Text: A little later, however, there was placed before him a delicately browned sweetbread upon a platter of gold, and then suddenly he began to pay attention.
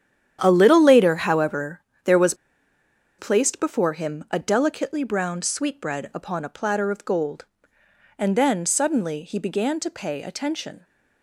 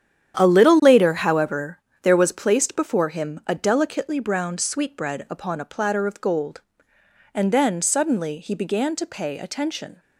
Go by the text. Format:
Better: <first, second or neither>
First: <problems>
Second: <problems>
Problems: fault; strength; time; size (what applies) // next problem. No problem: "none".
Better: second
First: starts louder than the rest; strong; until 1.4 s; 9.5 dB // pauses between "was" and "placed"; noticeable; at 2.3 s; 0.84 s long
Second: starts louder than the rest; strong; until 1.4 s; 9.5 dB